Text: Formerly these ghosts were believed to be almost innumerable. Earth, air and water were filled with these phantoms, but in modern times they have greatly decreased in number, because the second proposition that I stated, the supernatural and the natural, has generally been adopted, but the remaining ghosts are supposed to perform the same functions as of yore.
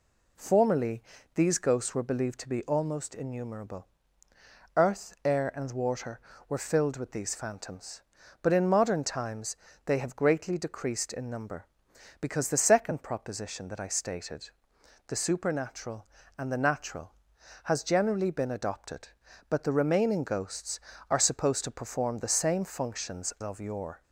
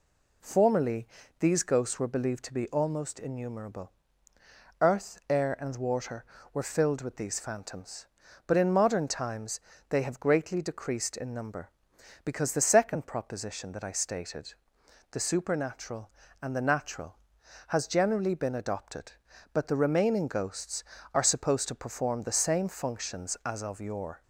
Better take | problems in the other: second | pauses between "Formerly" and "these"; slight; at 1.0 s; 0.32 s long; slight in the second // pauses between "times" and "they"; slight; at 9.5 s; 0.30 s long; slight in the second // skips "as"; at 23.3 s

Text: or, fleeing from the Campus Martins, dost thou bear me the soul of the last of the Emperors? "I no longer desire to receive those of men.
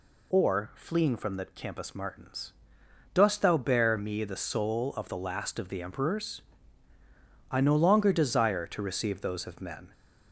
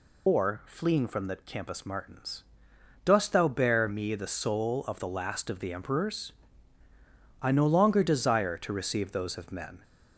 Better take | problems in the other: first | loses the start of "or"; at 0.2 s; 50 ms

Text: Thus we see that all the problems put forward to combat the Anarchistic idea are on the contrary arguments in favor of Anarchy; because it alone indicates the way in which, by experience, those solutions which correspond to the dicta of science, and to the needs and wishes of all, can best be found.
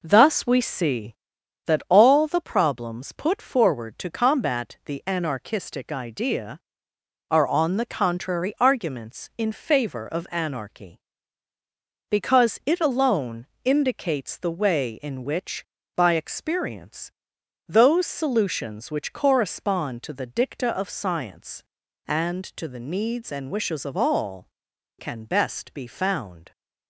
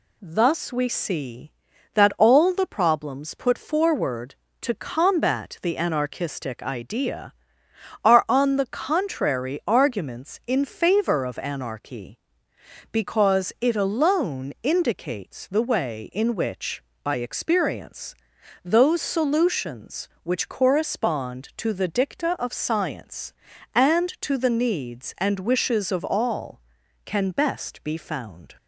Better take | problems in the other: second | starts louder than the rest; noticeable; until 1.3 s; 5 dB // pauses between "alone" and "indicates"; slight; at 13.4 s; 0.16 s long

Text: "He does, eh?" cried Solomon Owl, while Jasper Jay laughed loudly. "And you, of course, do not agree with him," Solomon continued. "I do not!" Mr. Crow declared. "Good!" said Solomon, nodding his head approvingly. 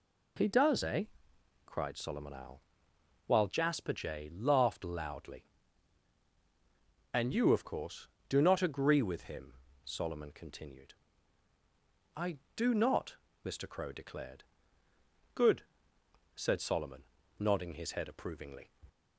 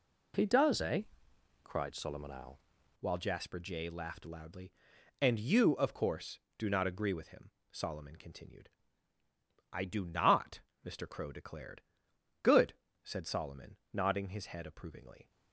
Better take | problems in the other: first | changes voice at "while"; from 3.0 s on; 12.3 s long

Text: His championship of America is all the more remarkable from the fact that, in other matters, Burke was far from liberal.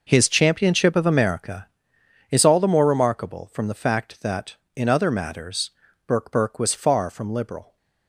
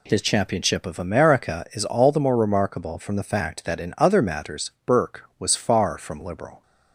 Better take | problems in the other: second | says "Burke" twice; at 6.2 s

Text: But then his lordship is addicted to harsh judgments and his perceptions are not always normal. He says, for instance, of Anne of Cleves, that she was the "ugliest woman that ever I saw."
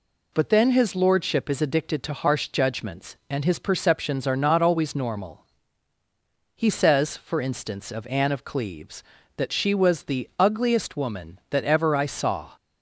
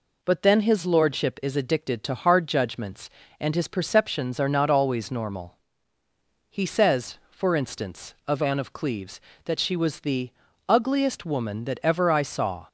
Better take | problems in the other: first | says "hard" for "harsh"; at 2.1 s // pauses between "the" and "ugliest"; at 10.2 s; 0.38 s long

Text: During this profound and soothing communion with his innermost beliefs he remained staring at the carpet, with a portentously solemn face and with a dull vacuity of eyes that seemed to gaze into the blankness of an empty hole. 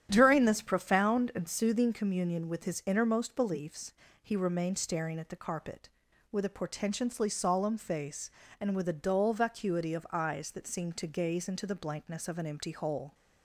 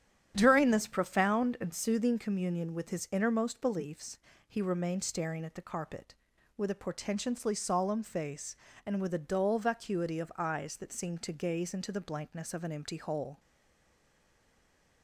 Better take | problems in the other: first | starts louder than the rest; strong; until 1.3 s; 10 dB; strong in the first // pauses between "beliefs" and "he"; slight; at 4.1 s; 0.28 s long; slight in the first // stays silent after the last word; noticeable; from 13.3 s on; 1.7 s long

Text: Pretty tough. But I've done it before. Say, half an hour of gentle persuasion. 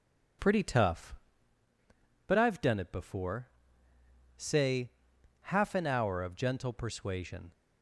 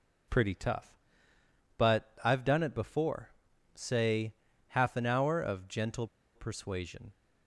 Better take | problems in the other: first | pauses between "gentle" and "persuasion"; slight; at 6.0 s; 0.28 s long

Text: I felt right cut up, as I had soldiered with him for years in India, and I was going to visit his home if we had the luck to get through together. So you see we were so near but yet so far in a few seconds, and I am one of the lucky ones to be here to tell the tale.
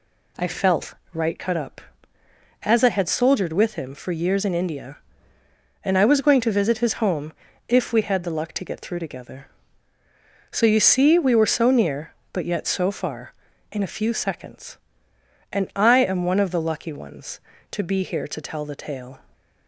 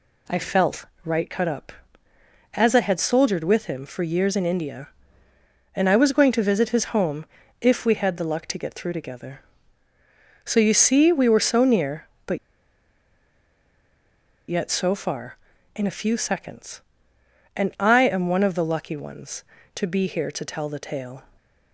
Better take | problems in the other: first | pauses between "felt" and "right"; slight; at 0.8 s; 0.18 s long; slight in the first // pauses between "home" and "if"; slight; at 7.2 s; 0.36 s long; slight in the first // pauses between "but" and "yet"; strong; at 12.3 s; 2.1 s long

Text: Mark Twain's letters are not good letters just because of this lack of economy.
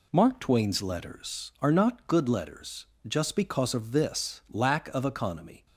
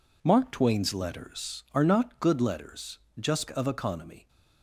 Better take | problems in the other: first | pauses between "letters" and "just"; slight; at 2.9 s; 0.20 s long; slight in the first // skips "because of this lack"; at 3.5 s

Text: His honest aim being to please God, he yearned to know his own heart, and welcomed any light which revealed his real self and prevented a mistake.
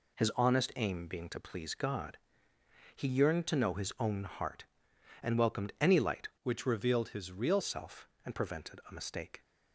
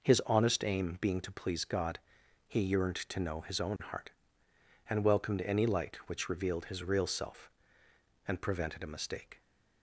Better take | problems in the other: second | changes voice from "which" to "real"; from 6.4 to 7.6 s; 1.2 s long

